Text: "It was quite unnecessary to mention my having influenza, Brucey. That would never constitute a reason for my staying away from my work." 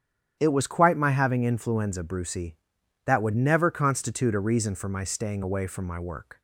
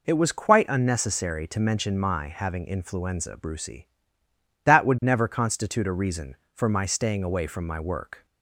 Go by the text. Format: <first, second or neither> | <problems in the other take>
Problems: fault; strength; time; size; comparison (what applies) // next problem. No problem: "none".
second | starts louder than the rest; strong; until 1.4 s; 10 dB // skips "unnecessary to mention"; at 0.9 s